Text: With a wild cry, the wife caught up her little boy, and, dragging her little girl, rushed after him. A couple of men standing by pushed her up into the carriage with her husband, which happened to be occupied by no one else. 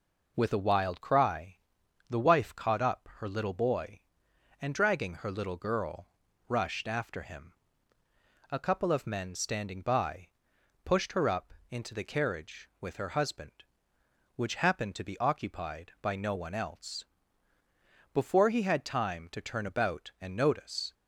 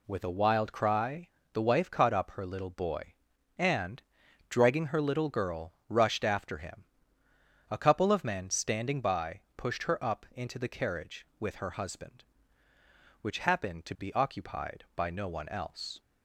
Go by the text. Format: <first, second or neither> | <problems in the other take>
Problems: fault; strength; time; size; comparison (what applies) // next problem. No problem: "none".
second | pauses between "by" and "pushed"; noticeable; at 10.2 s; 0.56 s long; slight in the second // pauses between "up" and "into"; slight; at 11.5 s; 0.18 s long // goes on to say "Before he had time to turn about and notice"; strong; from 18.1 s on; 2.8 s long